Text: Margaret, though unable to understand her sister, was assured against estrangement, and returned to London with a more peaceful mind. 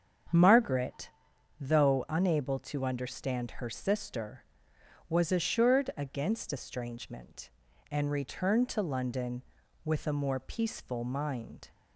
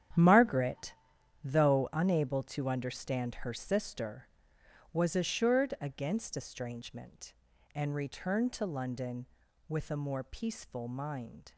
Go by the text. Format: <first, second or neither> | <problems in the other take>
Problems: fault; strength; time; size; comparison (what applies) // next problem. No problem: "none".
first | gets quieter; strong; throughout; 12 dB // starts louder than the rest; strong; until 1.6 s; 10 dB; strong in the first